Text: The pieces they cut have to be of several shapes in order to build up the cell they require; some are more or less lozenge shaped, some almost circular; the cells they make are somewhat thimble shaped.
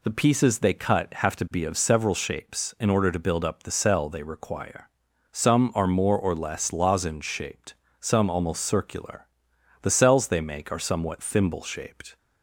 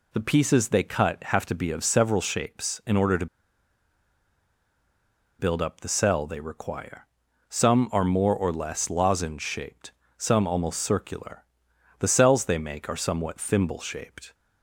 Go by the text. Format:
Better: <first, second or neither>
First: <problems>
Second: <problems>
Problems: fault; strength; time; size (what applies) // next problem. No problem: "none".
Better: first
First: none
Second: pauses between "to" and "build"; strong; at 3.2 s; 2.1 s long